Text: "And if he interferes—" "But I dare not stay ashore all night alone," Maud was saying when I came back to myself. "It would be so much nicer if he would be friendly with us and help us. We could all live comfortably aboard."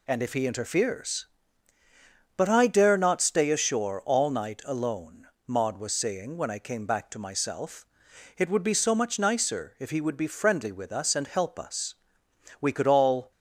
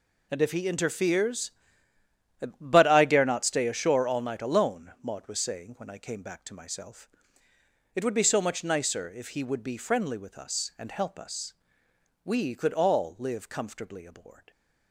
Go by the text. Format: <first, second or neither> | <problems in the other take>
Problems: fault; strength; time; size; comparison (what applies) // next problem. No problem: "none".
second | stops before "live comfortably aboard"; at 13.3 s